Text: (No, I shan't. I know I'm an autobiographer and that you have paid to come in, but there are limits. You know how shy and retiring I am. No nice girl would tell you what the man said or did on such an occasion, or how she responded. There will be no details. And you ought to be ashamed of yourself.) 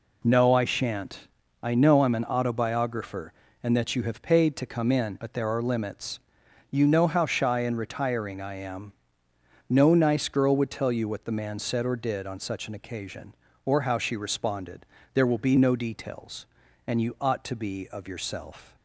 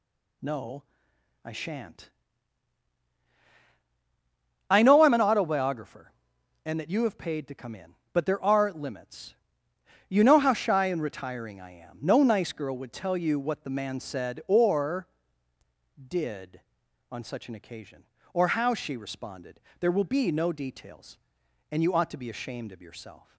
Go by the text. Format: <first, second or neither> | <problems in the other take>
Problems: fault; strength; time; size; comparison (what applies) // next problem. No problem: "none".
second | skips "ashamed"; at 17.8 s